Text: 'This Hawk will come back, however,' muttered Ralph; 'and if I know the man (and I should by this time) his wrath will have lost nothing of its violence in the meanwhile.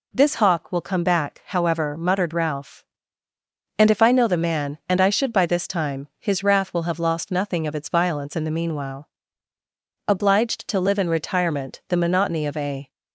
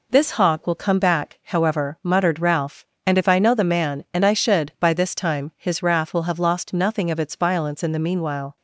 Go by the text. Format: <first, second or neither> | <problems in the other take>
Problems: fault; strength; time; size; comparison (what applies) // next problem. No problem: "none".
second | goes on to say "Obliged to live in retirement the monotony of a"; strong; from 10.0 s on; 2.8 s long